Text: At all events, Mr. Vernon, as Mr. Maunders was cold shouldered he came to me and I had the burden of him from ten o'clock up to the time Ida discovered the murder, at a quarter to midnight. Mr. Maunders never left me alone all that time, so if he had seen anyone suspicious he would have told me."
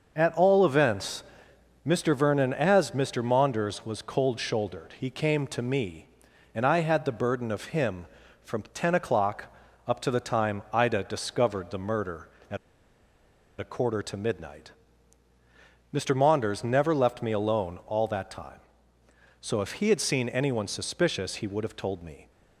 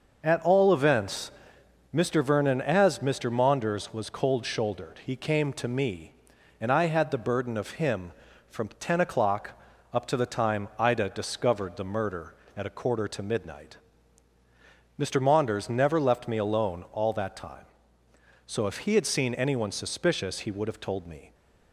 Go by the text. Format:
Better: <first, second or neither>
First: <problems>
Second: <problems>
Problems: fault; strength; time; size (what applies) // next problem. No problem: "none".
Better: second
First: starts louder than the rest; noticeable; until 1.1 s; 6 dB // pauses between "o'clock" and "up"; slight; at 9.5 s; 0.32 s long // pauses between "at" and "a"; at 12.5 s; 1.0 s long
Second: starts louder than the rest; noticeable; until 1.2 s; 6 dB // pauses between "o'clock" and "up"; slight; at 9.5 s; 0.32 s long